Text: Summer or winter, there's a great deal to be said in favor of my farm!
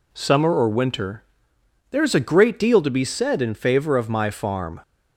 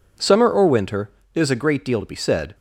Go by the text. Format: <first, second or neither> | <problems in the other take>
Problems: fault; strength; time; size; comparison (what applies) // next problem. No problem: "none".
first | stops before "in favor of my farm"; at 2.5 s